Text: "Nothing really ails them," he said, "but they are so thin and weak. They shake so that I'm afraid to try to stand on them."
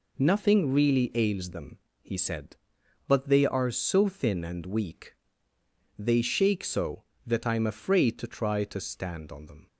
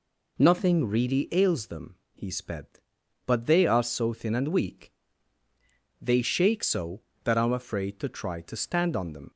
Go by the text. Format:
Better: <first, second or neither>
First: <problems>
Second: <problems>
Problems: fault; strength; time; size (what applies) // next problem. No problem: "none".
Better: first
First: none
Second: says "sped" for "said"; at 2.3 s